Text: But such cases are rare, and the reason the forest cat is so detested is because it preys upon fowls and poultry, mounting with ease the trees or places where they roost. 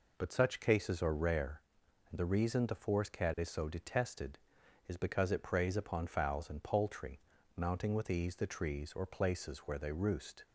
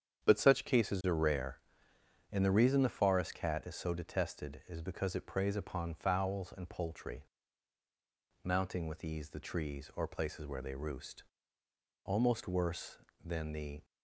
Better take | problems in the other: first | starts louder than the rest; strong; until 1.2 s; 8.5 dB // goes on to say "Almost worse than the"; strong; from 12.0 s on; 1.8 s long

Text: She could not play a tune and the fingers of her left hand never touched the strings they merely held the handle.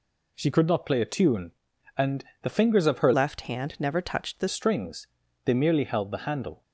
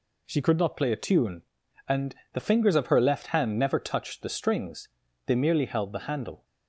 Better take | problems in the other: second | pauses between "and" and "the"; slight; at 2.2 s; 0.18 s long; slight in the second // changes voice from "left" to "the"; from 3.1 to 4.4 s; 1.3 s long // pauses between "strings" and "they"; at 5.0 s; 0.38 s long; also in the second

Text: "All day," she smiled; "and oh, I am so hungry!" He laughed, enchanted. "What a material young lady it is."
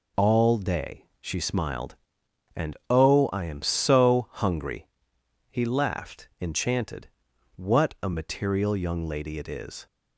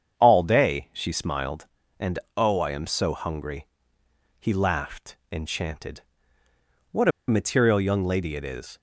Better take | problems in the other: first | starts louder than the rest; strong; until 1.2 s; 7.5 dB // pauses between "and" and "oh"; slight; at 2.1 s; 0.20 s long // pauses between "What" and "a"; slight; at 7.0 s; 0.18 s long

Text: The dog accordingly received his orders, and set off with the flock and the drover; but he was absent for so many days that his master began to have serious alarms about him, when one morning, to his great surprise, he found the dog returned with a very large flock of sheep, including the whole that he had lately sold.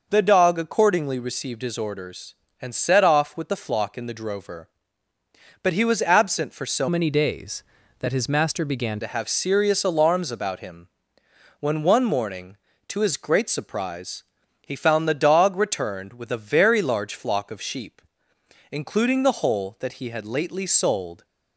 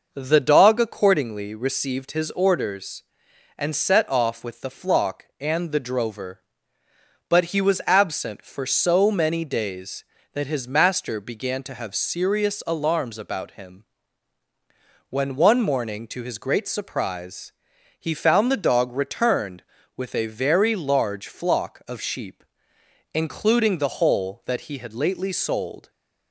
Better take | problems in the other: second | changes voice from "many" to "began"; from 6.8 to 8.9 s; 2.1 s long

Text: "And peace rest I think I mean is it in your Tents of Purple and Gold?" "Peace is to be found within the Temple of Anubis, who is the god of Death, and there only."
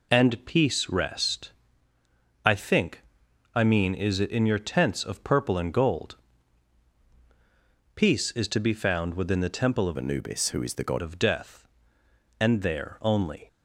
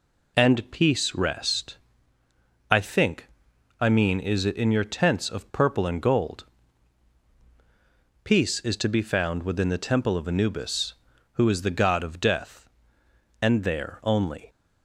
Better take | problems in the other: second | pauses between "rest" and "I"; noticeable; at 1.5 s; 0.94 s long; noticeable in the second // pauses between "think" and "I"; noticeable; at 3.0 s; 0.54 s long; noticeable in the second // changes voice from "Anubis" to "god"; from 9.9 to 11.0 s; 1.1 s long

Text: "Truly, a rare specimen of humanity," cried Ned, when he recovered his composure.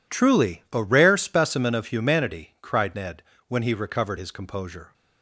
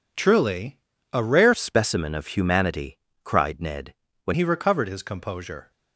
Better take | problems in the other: first | changes voice from "specimen" to "when"; from 1.5 to 4.3 s; 2.8 s long

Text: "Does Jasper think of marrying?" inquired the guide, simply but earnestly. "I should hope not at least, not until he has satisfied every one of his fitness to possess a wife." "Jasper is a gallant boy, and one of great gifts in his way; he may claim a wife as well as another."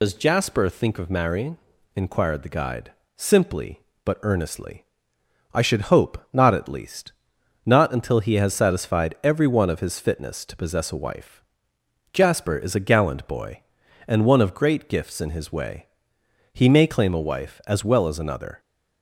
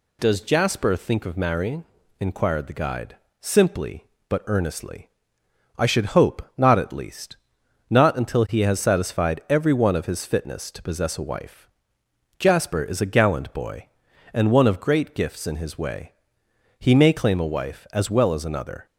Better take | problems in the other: second | loses the start of "Does"; at 0.0 s; 85 ms // pauses between "hope" and "not"; slight; at 6.1 s; 0.16 s long; slight in the second

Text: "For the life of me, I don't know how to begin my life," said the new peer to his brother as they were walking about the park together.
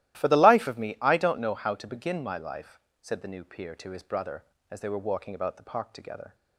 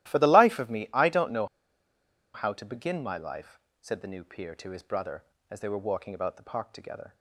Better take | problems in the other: first | starts louder than the rest; strong; until 1.1 s; 14.5 dB; strong in the first // pauses between "know" and "how"; noticeable; at 1.4 s; 0.87 s long

